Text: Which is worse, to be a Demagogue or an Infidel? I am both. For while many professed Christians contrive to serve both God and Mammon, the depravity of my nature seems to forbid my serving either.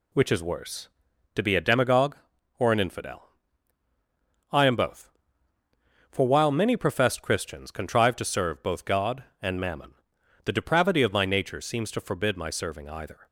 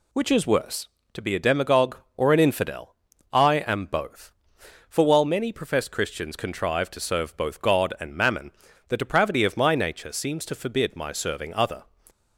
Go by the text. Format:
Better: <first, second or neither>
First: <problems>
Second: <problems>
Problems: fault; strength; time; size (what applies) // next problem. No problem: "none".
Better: first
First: none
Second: says "other" for "either"; at 11.5 s